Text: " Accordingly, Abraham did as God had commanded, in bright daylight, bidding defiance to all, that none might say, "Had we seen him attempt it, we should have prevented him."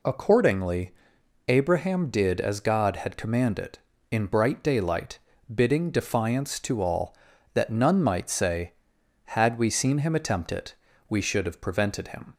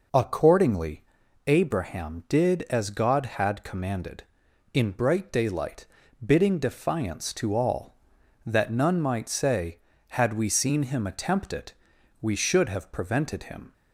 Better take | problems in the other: neither | none

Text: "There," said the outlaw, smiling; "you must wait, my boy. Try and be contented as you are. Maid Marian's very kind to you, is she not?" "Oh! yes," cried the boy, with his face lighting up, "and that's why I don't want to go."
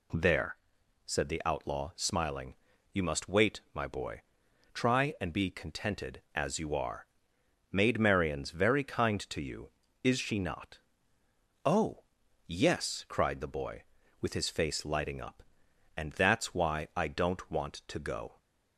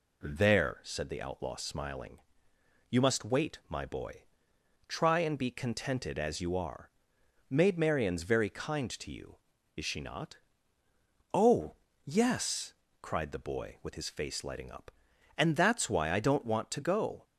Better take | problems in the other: neither | none

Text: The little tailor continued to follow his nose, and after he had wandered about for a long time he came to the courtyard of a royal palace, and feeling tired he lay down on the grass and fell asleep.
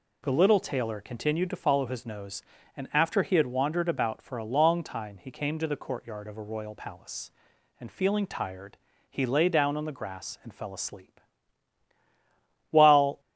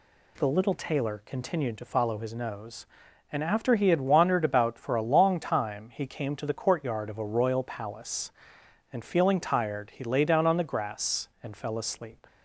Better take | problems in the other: second | pauses between "tired" and "he"; slight; at 8.7 s; 0.32 s long // goes on to say "While"; from 12.6 s on; 0.50 s long

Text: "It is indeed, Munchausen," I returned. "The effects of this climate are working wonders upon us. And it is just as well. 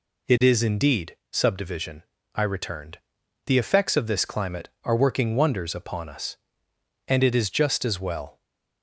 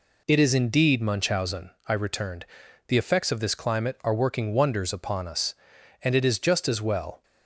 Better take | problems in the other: second | says "Subdivision" for "Munchausen"; at 1.3 s // stays silent after the last word; slight; from 8.3 s on; 0.5 s long

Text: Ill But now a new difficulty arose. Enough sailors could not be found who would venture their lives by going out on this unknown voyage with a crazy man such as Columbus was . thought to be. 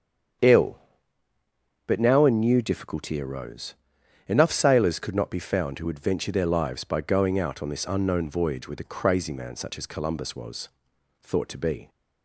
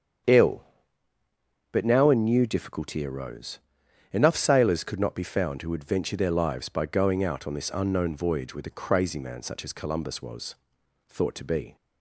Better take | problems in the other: neither | starts louder than the rest; strong; the same in both

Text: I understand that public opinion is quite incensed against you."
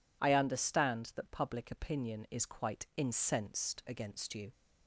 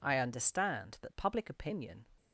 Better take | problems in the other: first | stops before "is quite incensed against you"; at 2.1 s

